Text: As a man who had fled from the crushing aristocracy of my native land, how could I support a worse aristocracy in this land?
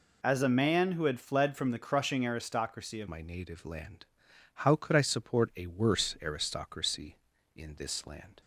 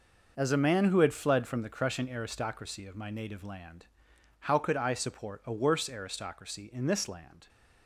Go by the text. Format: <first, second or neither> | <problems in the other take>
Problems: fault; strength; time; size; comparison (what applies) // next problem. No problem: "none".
second | changes voice at "my"; from 3.0 s on; 5.4 s long